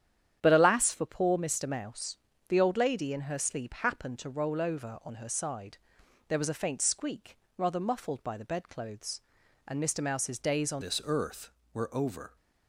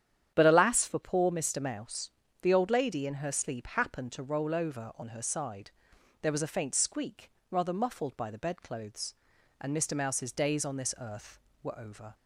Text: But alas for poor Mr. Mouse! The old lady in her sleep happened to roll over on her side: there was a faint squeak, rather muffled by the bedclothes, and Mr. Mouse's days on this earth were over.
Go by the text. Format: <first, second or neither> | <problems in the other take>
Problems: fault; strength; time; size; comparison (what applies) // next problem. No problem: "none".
second | starts louder than the rest; strong; until 1.4 s; 9 dB; strong in the second // changes voice at "this"; from 10.8 s on; 1.5 s long